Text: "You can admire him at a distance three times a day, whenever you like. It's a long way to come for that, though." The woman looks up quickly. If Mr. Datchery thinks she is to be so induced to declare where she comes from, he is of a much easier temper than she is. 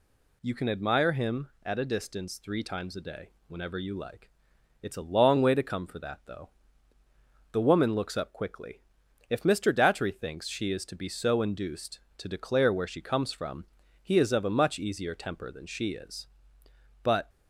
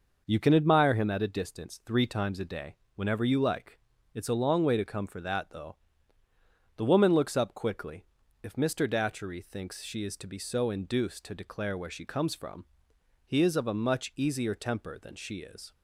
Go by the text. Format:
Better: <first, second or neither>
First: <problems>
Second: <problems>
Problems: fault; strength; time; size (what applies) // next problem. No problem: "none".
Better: second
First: goes on to say "But"; slight; from 17.0 s on; 0.26 s long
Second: none